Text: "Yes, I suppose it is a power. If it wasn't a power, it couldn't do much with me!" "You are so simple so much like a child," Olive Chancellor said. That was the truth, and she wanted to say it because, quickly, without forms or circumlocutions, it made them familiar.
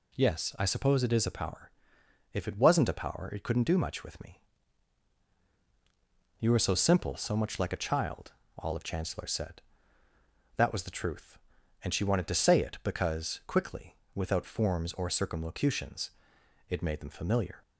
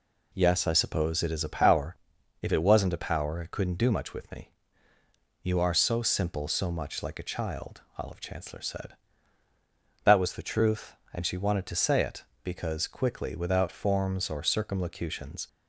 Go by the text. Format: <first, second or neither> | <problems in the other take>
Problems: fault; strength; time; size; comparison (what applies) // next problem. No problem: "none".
first | stops before "it made them familiar"; at 15.4 s